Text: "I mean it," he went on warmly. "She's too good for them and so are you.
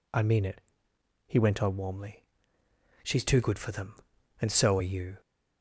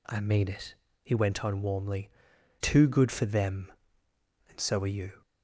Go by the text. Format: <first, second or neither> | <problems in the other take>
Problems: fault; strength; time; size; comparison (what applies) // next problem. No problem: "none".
first | skips "She's"; at 2.3 s